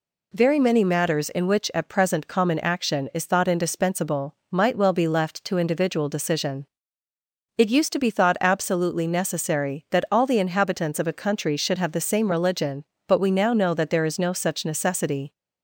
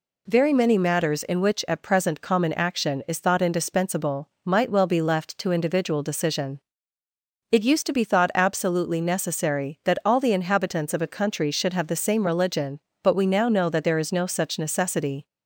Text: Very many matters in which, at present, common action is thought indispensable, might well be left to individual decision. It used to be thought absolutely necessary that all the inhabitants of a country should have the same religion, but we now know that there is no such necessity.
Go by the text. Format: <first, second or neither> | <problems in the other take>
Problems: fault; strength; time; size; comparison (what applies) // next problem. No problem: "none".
neither | none